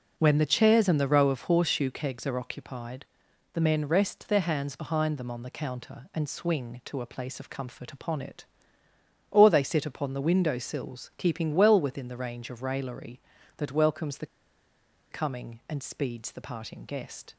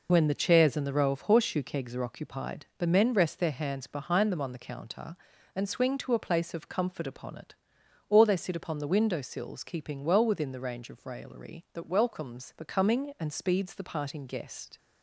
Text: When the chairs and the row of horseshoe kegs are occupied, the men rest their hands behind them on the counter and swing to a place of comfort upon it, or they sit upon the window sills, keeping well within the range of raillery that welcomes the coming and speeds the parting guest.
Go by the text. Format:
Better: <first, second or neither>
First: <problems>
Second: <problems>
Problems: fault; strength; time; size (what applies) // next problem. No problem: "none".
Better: second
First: pauses between "the" and "coming"; noticeable; at 14.2 s; 0.85 s long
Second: none